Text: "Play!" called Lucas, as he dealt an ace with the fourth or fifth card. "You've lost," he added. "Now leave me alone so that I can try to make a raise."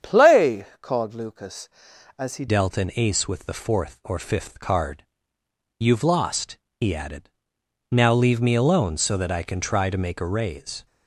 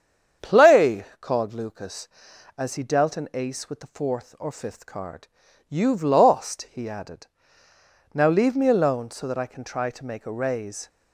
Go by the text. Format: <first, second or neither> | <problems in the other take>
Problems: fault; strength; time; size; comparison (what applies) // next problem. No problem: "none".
second | starts louder than the rest; strong; until 1.1 s; 8 dB; strong in the second // changes voice at "dealt"; from 2.4 s on; 8.4 s long